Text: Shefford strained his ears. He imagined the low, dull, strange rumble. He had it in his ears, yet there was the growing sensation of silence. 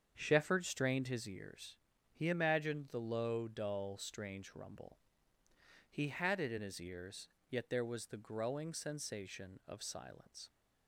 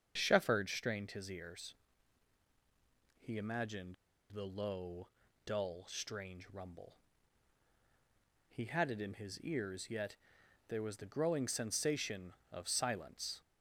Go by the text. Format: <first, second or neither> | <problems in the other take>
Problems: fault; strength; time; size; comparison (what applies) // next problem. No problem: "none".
first | starts louder than the rest; strong; until 1.1 s; 7 dB; strong in the first // pauses between "imagined" and "the"; at 3.9 s; 0.38 s long // pauses between "yet" and "there"; noticeable; at 10.1 s; 0.50 s long